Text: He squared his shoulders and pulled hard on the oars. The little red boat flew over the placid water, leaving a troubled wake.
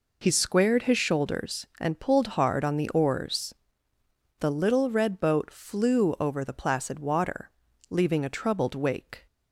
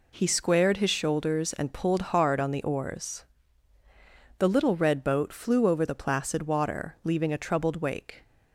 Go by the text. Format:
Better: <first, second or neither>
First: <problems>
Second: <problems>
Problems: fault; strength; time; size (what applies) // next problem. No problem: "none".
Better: neither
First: none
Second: none